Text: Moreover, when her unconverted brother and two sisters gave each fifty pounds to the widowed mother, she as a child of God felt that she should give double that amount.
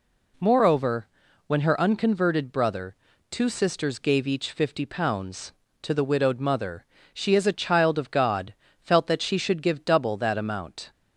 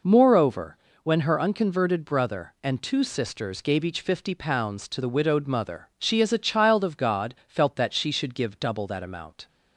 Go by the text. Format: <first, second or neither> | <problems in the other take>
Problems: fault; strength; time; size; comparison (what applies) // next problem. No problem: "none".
second | skips "and"; at 3.1 s // pauses between "God" and "felt"; slight; at 8.5 s; 0.28 s long